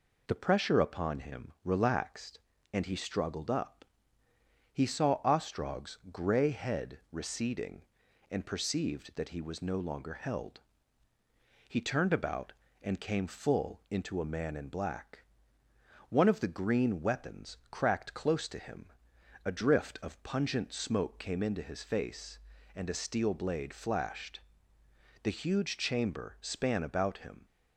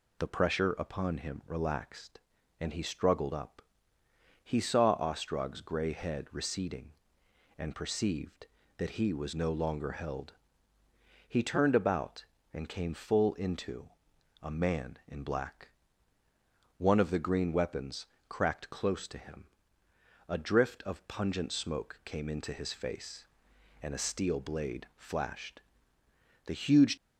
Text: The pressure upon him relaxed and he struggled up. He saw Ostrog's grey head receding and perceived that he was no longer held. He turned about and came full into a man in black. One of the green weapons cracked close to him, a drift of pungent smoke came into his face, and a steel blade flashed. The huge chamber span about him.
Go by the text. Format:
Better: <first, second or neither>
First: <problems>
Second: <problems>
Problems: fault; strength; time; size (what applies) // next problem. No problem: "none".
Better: first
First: none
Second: pauses between "into" and "a"; noticeable; at 13.8 s; 0.52 s long // pauses between "weapons" and "cracked"; slight; at 18.0 s; 0.24 s long // stops before "chamber span about him"; at 26.9 s